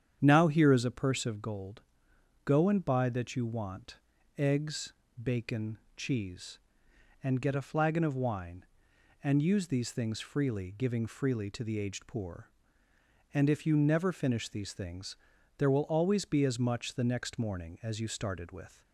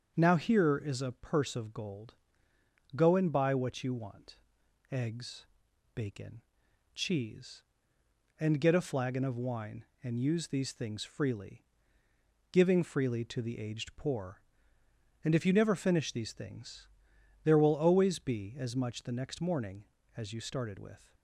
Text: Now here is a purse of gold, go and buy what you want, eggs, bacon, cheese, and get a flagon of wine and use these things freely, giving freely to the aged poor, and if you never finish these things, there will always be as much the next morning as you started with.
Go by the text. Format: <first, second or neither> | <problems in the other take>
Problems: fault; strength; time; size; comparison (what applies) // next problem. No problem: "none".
second | starts louder than the rest; strong; until 1.2 s; 8.5 dB; also in the second // says "that" for "what"; at 3.0 s